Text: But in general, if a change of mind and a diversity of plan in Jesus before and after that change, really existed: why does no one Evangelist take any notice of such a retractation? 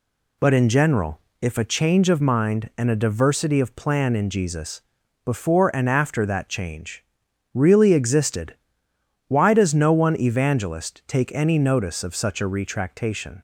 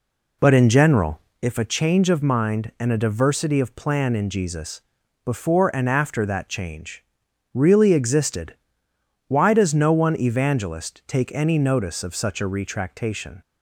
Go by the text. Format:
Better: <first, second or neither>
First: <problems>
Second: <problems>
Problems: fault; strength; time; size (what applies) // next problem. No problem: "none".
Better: first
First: pauses between "Jesus" and "before"; at 4.8 s; 0.44 s long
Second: starts louder than the rest; slight; until 1.4 s; 3 dB // pauses between "Jesus" and "before"; at 4.8 s; 0.44 s long